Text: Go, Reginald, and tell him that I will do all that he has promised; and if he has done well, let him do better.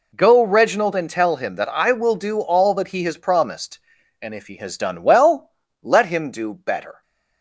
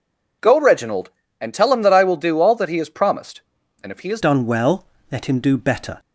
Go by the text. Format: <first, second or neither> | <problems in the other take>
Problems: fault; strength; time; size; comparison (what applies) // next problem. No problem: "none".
first | changes voice at "done"; from 4.2 s on; 1.7 s long